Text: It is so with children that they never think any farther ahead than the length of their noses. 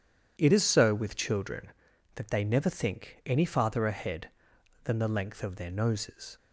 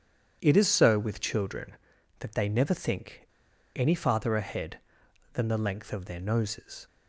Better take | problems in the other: first | pauses between "think" and "any"; noticeable; at 3.2 s; 0.50 s long

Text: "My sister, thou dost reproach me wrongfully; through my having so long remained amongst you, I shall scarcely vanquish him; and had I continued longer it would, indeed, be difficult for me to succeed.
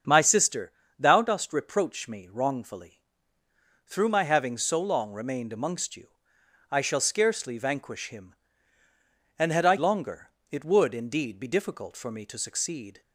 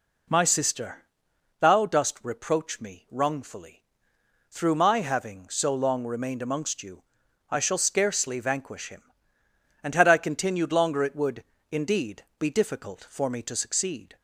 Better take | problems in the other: second | starts louder than the rest; strong; until 1.3 s; 7 dB // skips "continued"; at 9.7 s // pauses between "longer" and "it"; slight; at 10.2 s; 0.22 s long

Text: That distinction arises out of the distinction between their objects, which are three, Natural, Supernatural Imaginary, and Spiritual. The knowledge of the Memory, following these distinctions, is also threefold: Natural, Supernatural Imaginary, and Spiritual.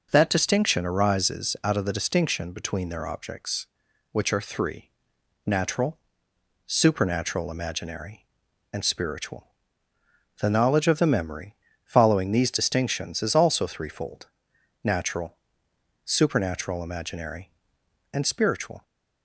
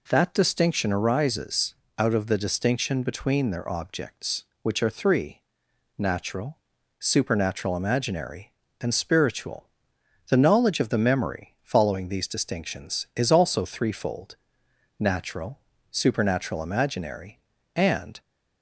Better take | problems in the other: first | pauses between "arises" and "out"; slight; at 1.7 s; 0.24 s long // stops before "Spiritual"; at 18.2 s

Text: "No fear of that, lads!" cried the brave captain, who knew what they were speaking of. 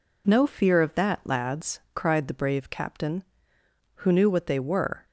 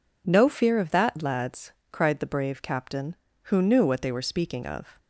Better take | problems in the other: second | stops before "speaking of"; at 5.0 s

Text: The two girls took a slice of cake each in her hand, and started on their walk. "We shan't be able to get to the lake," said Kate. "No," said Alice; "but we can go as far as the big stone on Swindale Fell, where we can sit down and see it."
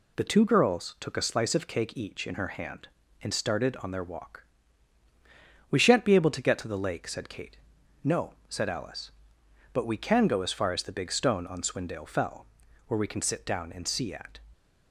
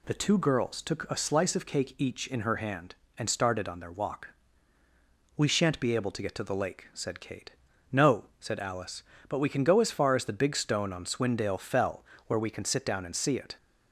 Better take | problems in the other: second | says "at" for "it"; at 14.1 s

